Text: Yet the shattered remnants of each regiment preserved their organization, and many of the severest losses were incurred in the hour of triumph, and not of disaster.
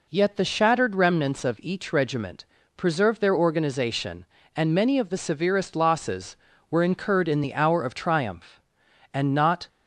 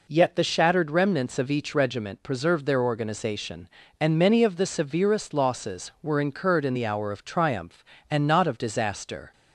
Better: second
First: pauses between "regiment" and "preserved"; slight; at 2.4 s; 0.30 s long // stops before "of disaster"; at 9.6 s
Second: none

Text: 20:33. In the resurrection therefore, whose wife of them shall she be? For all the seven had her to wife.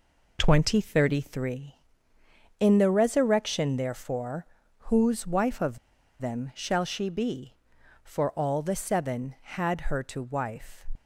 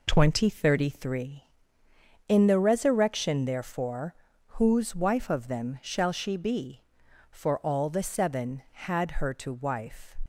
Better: second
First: pauses between "of" and "them"; at 5.7 s; 0.43 s long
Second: none

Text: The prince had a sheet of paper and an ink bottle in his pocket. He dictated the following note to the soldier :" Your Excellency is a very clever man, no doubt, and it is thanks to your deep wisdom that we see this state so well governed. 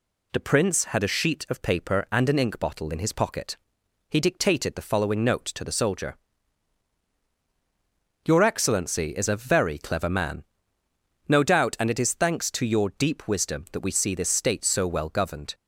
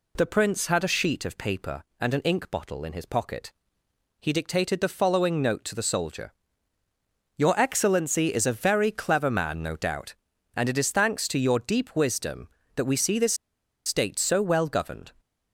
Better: first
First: none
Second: pauses between "this" and "state"; noticeable; at 13.3 s; 0.51 s long

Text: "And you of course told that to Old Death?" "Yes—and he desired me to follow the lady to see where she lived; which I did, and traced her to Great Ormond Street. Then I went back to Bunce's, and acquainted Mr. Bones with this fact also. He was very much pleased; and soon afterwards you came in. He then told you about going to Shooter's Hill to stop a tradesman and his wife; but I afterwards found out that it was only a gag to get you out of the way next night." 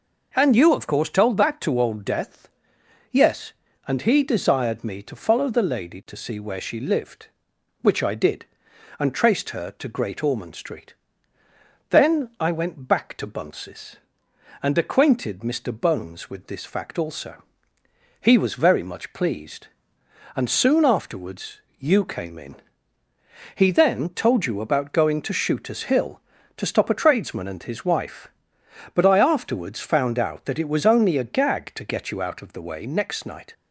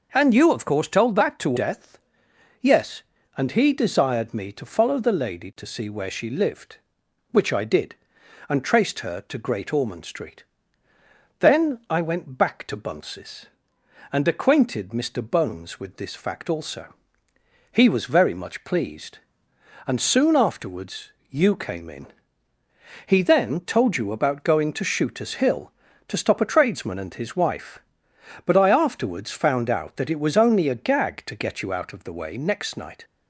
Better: first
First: pauses between "afterwards" and "you"; slight; at 21.6 s; 0.18 s long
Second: skips "Old"; at 1.5 s // pauses between "afterwards" and "you"; slight; at 21.1 s; 0.18 s long

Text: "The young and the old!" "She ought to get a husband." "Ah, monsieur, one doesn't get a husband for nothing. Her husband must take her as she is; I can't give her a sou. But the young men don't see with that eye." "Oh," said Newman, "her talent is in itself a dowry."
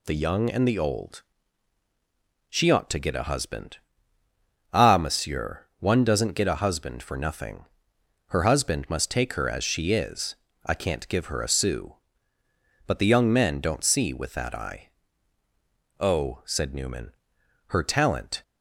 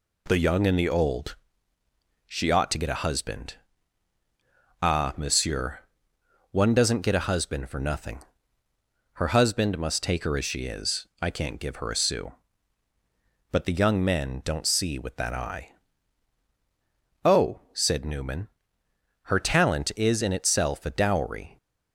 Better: second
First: stops before "is in itself a dowry"; at 18.4 s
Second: none

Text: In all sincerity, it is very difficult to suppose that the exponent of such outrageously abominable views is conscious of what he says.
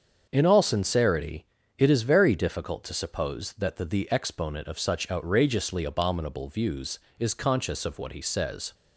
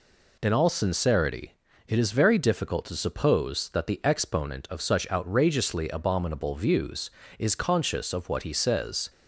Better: second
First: starts louder than the rest; until 1.3 s; 7 dB // says "the" twice; at 3.8 s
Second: none

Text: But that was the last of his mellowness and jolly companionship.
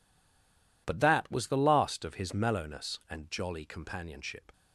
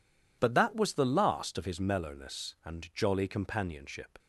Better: second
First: stays silent before the first word; slight; until 0.8 s; 0.8 s long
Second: none

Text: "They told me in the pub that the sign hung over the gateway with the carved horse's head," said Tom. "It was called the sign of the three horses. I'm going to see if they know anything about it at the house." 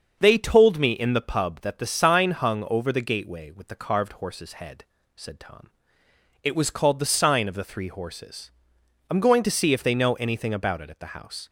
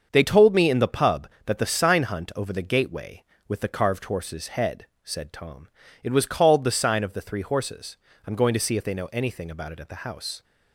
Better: first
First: starts louder than the rest; until 1.2 s; 6.5 dB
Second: starts louder than the rest; until 1.1 s; 6.5 dB // says "hunt" for "hung"; at 2.0 s

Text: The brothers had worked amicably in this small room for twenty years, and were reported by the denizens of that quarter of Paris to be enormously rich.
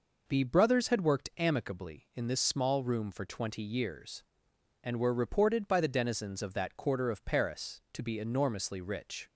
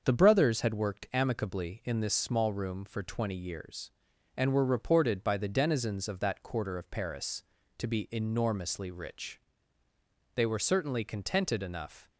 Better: first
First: none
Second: starts louder than the rest; until 1.0 s; 6.5 dB // goes on to say "They were certainly contented enough"; strong; from 10.3 s on; 1.7 s long

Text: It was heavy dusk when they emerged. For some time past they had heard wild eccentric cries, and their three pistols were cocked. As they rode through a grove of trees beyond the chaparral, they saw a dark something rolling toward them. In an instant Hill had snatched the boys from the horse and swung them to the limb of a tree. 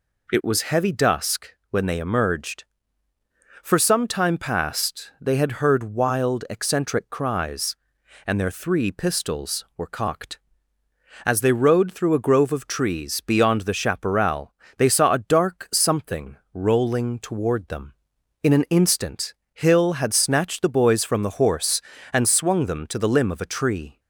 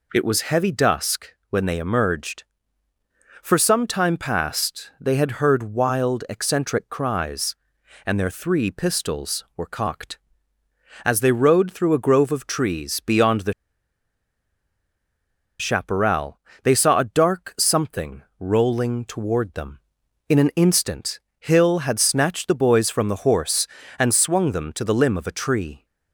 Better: first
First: pauses between "dusk" and "when"; slight; at 1.5 s; 0.16 s long // pauses between "something" and "rolling"; slight; at 16.3 s; 0.16 s long // pauses between "instant" and "Hill"; slight; at 19.3 s; 0.22 s long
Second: pauses between "dusk" and "when"; slight; at 1.3 s; 0.16 s long // pauses between "the" and "chaparral"; strong; at 13.5 s; 2.0 s long // pauses between "something" and "rolling"; slight; at 18.2 s; 0.16 s long // pauses between "instant" and "Hill"; slight; at 21.1 s; 0.22 s long

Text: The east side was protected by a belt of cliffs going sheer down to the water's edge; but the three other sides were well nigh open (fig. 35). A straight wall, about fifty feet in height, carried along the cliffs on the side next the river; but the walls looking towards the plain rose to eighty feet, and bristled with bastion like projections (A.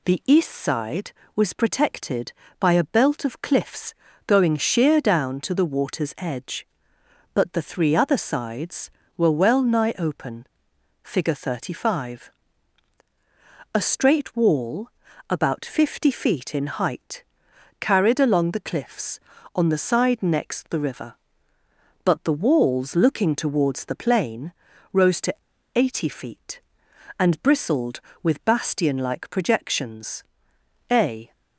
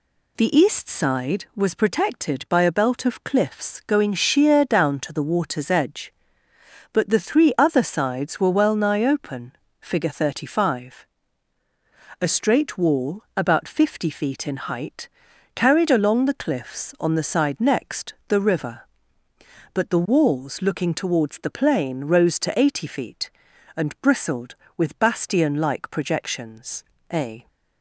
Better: second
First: pauses between "cliffs" and "going"; slight; at 3.9 s; 0.32 s long // pauses between "plain" and "rose"; at 24.5 s; 0.40 s long // pauses between "to" and "eighty"; at 25.3 s; 0.42 s long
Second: none

